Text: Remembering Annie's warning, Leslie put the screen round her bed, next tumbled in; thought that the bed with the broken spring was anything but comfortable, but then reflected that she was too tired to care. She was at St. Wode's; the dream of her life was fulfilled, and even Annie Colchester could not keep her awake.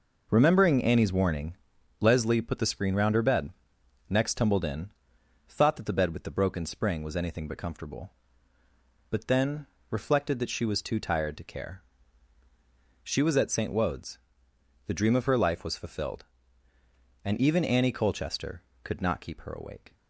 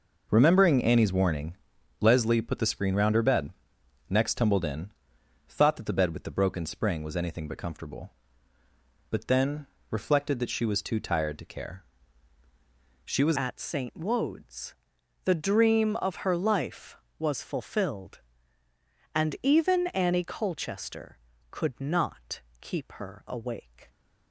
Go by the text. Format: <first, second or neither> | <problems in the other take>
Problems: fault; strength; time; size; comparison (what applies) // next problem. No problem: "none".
first | pauses between "then" and "reflected"; slight; at 9.6 s; 0.24 s long; slight in the first // changes voice at "at"; from 13.3 s on; 10.5 s long // pauses between "not" and "keep"; slight; at 22.4 s; 0.18 s long